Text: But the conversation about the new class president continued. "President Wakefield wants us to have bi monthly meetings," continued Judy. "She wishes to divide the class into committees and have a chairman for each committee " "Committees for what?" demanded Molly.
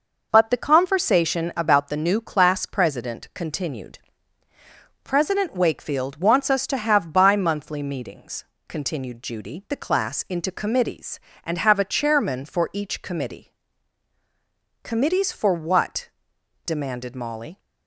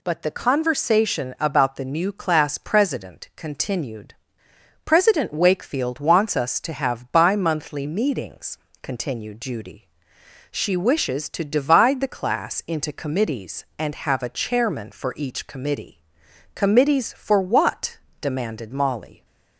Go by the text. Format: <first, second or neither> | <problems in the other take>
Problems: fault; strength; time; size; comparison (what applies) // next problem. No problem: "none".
second | skips "She wishes to divide"; at 9.6 s